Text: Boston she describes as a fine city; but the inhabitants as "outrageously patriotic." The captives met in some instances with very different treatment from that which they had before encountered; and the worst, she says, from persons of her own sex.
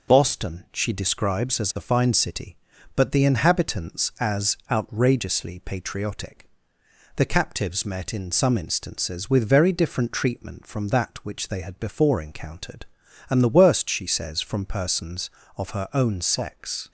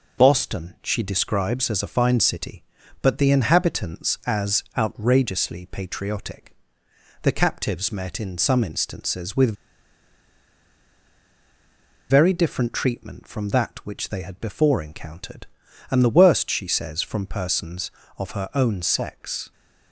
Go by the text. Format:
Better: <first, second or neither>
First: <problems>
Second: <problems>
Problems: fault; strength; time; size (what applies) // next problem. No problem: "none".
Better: first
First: none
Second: pauses between "with" and "very"; strong; at 9.5 s; 2.5 s long